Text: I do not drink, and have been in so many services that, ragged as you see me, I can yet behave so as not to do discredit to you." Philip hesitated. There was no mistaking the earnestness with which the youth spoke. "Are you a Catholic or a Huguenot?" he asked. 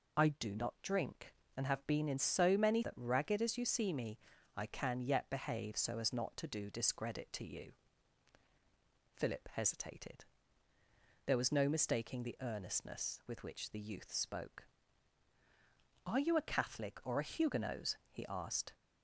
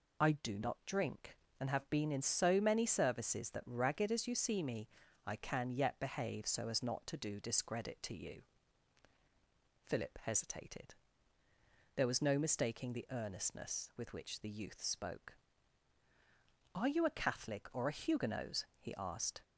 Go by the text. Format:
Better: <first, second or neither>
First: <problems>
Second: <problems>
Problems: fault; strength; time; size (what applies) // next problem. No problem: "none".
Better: second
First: skips "services"; at 2.8 s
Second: none